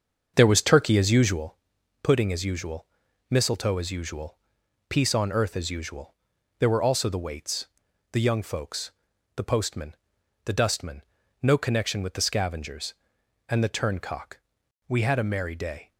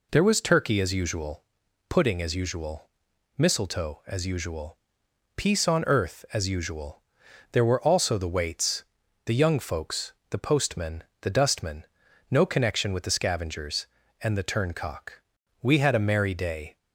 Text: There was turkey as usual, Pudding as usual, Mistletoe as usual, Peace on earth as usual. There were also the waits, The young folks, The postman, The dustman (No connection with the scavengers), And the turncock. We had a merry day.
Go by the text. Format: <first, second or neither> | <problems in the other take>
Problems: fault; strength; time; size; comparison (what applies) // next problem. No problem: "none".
second | starts louder than the rest; until 1.5 s; 6.5 dB